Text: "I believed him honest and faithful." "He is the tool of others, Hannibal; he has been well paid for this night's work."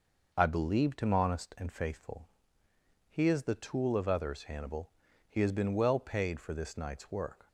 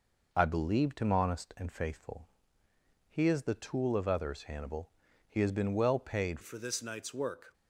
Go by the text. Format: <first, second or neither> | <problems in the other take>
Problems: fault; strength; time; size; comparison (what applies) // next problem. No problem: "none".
first | changes voice at "for"; from 6.4 s on; 1.1 s long